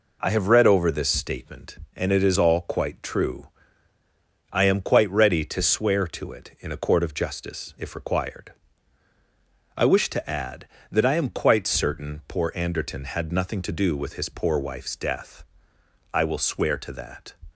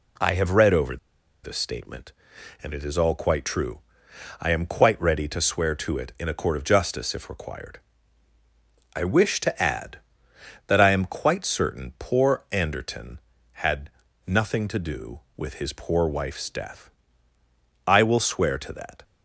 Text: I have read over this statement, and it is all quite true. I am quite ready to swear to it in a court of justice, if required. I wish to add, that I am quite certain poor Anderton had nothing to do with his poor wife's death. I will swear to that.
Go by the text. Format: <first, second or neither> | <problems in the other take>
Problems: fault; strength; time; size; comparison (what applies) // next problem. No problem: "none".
first | pauses between "over" and "this"; noticeable; at 0.9 s; 0.46 s long // pauses between "had" and "nothing"; at 13.8 s; 0.38 s long